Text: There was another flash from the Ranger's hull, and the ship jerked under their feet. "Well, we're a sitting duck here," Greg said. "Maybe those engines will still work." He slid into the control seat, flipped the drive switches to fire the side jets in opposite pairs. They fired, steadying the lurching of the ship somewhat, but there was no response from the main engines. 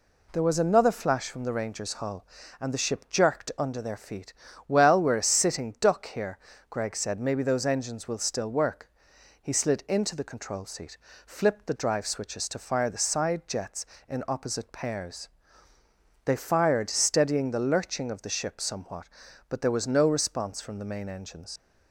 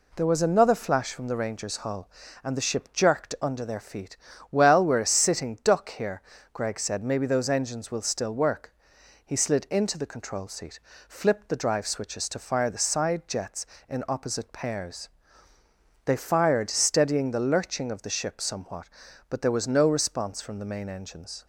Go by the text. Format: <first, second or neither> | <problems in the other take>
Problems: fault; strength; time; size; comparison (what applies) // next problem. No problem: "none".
second | leaves "engines" unfinished; at 21.5 s; 95 ms